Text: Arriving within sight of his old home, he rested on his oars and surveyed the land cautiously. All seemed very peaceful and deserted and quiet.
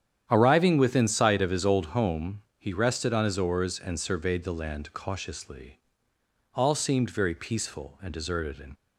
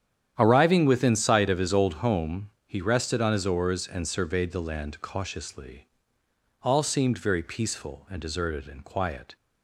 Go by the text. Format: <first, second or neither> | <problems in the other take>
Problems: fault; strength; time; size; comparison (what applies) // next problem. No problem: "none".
second | starts louder than the rest; strong; until 1.3 s; 9.5 dB; strong in the second // stops before "quiet"; at 8.7 s